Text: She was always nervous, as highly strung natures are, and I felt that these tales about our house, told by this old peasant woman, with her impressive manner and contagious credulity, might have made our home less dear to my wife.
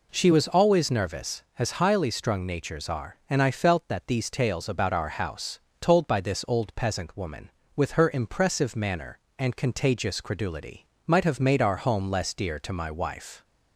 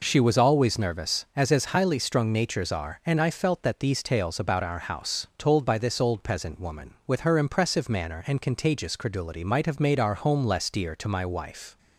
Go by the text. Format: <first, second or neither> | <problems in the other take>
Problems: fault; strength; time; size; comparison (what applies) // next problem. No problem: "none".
first | says "as" twice; at 1.5 s